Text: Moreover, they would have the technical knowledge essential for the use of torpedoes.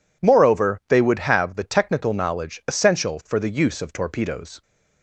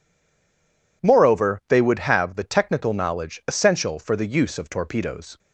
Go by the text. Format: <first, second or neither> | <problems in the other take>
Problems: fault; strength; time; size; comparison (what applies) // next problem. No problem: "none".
first | stays silent before the first word; until 1.0 s; 1.0 s long